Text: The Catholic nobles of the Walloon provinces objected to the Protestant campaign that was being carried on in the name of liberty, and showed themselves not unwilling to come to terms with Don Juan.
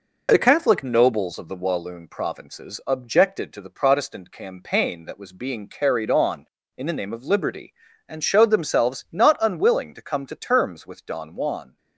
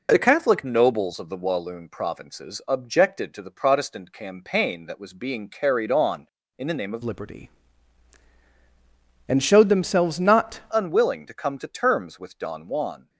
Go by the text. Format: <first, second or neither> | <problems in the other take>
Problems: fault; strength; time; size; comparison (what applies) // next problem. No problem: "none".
first | changes voice from "liberty" to "not"; from 7.0 to 10.5 s; 3.5 s long